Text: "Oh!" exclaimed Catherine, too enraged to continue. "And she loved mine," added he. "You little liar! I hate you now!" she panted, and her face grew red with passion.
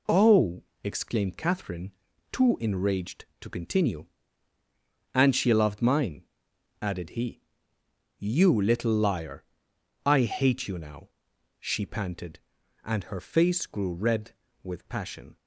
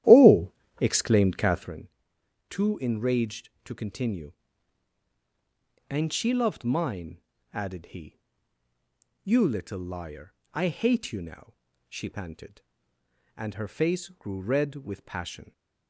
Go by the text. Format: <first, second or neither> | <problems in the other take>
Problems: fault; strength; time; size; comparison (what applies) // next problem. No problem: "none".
first | starts louder than the rest; strong; until 1.7 s; 13 dB